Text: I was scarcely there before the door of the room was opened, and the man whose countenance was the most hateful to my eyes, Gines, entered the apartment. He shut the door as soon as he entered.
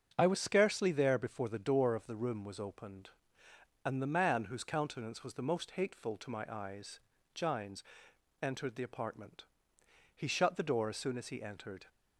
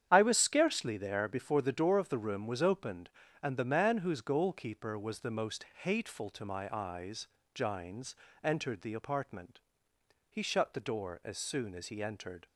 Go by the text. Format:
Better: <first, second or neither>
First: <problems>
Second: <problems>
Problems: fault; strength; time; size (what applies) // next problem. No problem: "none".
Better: first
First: starts louder than the rest; until 1.1 s; 7 dB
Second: starts louder than the rest; strong; until 1.1 s; 9 dB // says "goalkeeper" for "countenance"; at 4.2 s // pauses between "most" and "hateful"; slight; at 5.6 s; 0.16 s long